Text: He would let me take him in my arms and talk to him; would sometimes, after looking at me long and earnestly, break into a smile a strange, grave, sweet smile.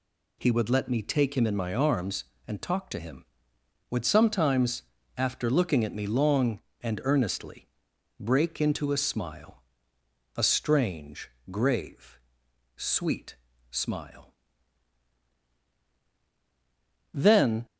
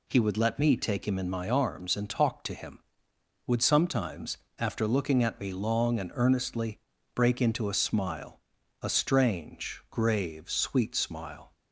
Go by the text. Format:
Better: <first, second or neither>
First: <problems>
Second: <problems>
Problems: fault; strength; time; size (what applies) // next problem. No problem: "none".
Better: second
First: pauses between "smile" and "a"; noticeable; at 9.5 s; 0.80 s long // pauses between "sweet" and "smile"; slight; at 13.3 s; 0.34 s long // goes on to say "Then"; from 17.1 s on; 0.52 s long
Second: pauses between "smile" and "a"; at 8.4 s; 0.40 s long